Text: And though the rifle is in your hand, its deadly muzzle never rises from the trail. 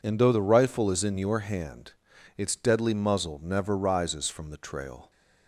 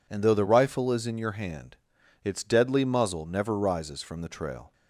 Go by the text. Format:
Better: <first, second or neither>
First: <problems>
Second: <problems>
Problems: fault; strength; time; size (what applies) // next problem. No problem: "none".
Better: neither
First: none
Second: none